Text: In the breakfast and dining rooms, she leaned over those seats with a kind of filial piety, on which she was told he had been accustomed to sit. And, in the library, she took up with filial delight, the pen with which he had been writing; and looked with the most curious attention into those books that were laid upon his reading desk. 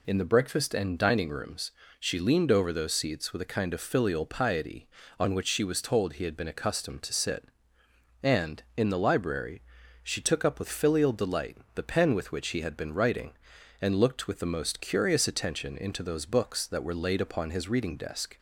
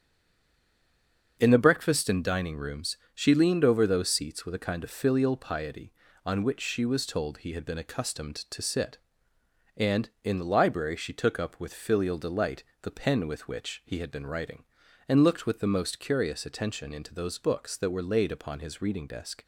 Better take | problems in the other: first | stays silent before the first word; noticeable; until 1.3 s; 1.3 s long // starts louder than the rest; until 2.4 s; 7 dB

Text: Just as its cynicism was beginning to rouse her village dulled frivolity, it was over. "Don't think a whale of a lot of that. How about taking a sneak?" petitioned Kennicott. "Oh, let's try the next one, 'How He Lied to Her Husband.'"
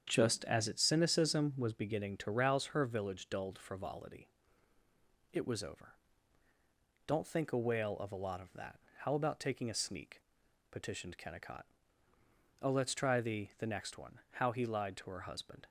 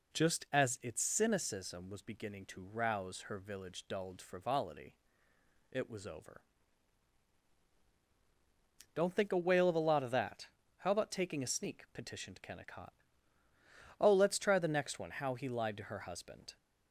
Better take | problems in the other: second | starts louder than the rest; strong; until 1.1 s; 8 dB // says "the" twice; at 13.5 s

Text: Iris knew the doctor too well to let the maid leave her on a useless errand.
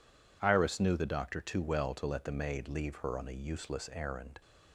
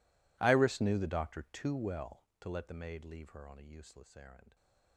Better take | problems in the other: first | gets quieter; strong; throughout; 26.5 dB

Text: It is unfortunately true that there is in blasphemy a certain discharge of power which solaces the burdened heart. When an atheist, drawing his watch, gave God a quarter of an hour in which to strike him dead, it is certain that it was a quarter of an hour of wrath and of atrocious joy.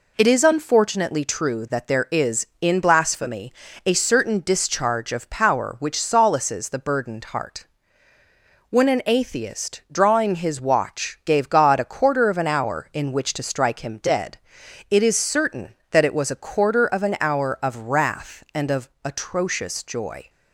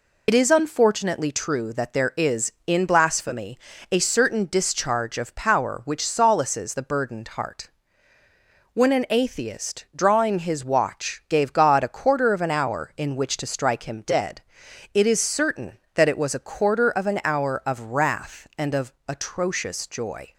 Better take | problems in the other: first | loses the start of "It"; at 0.2 s; 55 ms // pauses between "blasphemy" and "a"; slight; at 3.5 s; 0.34 s long; slight in the first

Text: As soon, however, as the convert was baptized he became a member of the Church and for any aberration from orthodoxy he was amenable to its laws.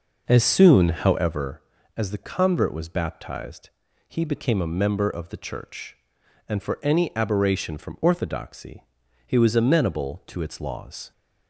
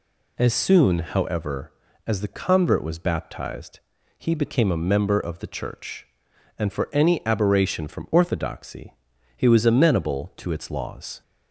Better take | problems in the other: second | starts louder than the rest; noticeable; until 1.6 s; 5.5 dB // pauses between "baptized" and "he"; at 3.6 s; 0.38 s long; also in the second // pauses between "orthodoxy" and "he"; at 8.8 s; 0.42 s long; also in the second

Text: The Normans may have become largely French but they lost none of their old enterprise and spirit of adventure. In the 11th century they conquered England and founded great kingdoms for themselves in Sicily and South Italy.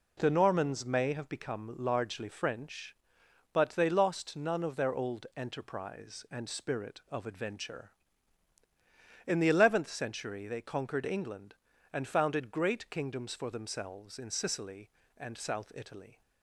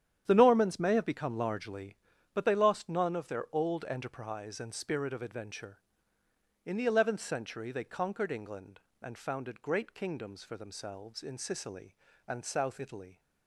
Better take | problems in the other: first | starts louder than the rest; strong; until 1.2 s; 9.5 dB // skips "French"; at 2.1 s

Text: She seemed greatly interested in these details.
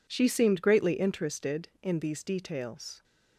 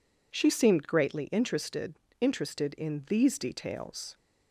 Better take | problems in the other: first | says "interested" twice; at 2.2 s

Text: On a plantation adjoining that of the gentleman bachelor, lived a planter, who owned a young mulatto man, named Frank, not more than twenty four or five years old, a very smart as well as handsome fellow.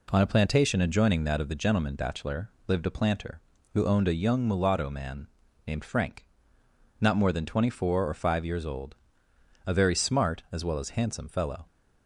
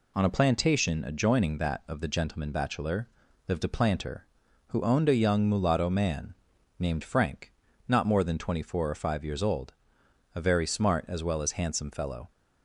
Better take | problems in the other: neither | none

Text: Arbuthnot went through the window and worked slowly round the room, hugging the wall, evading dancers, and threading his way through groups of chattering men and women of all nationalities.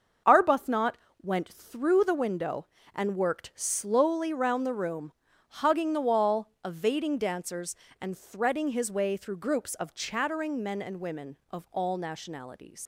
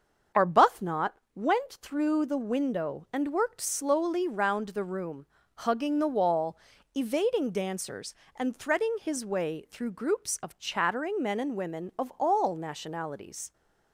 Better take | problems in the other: second | starts louder than the rest; until 1.5 s; 6.5 dB; strong in the second // pauses between "Arbuthnot" and "went"; slight; at 0.9 s; 0.28 s long; slight in the second // leaves "nationalities" unfinished; at 12.8 s; 90 ms

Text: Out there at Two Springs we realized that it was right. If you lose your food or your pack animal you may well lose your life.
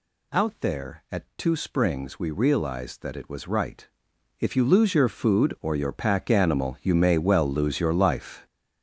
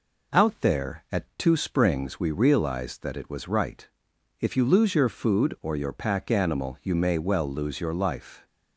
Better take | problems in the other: second | gets louder; strong; throughout; 9.5 dB

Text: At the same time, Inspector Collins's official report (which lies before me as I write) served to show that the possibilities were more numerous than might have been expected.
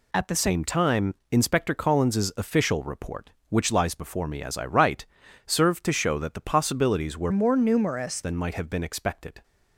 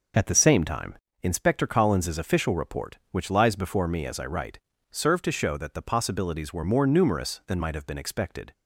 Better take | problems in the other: second | changes voice from "more" to "numerous"; from 7.3 to 8.2 s; 0.9 s long

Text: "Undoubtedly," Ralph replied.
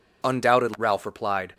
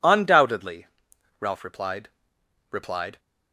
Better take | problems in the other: first | says "replied" twice; at 2.7 s

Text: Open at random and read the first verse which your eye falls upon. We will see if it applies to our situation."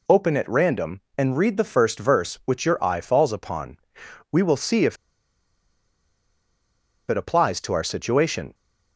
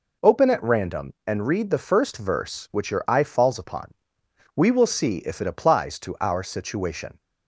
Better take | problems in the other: second | pauses between "if" and "it"; strong; at 4.9 s; 2.1 s long

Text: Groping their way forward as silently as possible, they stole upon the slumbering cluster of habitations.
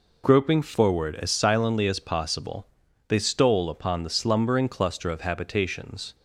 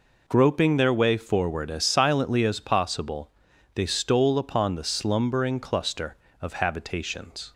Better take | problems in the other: second | skips "their way"; at 0.6 s

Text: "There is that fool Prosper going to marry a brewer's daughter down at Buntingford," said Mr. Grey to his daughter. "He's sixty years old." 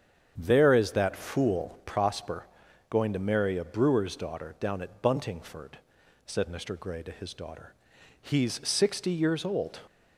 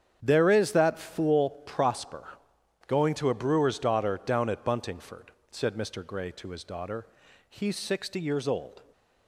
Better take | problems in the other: first | starts louder than the rest; strong; until 1.2 s; 9 dB; strong in the first // pauses between "fool" and "Prosper"; slight; at 1.4 s; 0.16 s long // pauses between "Prosper" and "going"; noticeable; at 2.2 s; 0.58 s long; also in the first // skips "marry"; at 3.2 s

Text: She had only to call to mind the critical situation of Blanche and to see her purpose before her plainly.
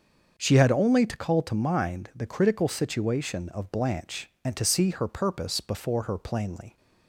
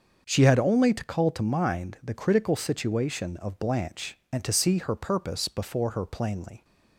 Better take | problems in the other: neither | starts louder than the rest; the same in both

